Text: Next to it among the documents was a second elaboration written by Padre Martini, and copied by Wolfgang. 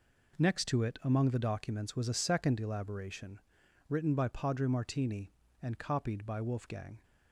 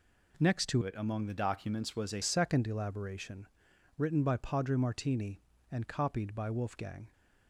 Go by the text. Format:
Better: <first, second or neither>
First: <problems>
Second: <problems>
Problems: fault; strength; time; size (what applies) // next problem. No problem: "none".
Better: first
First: pauses between "elaboration" and "written"; noticeable; at 3.3 s; 0.49 s long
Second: changes voice from "it" to "a"; from 0.8 to 2.2 s; 1.4 s long // pauses between "elaboration" and "written"; noticeable; at 3.4 s; 0.50 s long